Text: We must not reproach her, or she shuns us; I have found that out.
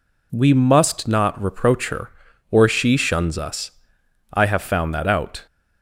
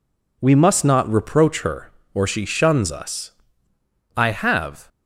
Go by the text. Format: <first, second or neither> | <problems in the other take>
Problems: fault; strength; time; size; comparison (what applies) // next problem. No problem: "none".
first | stops before "found that out"; at 4.8 s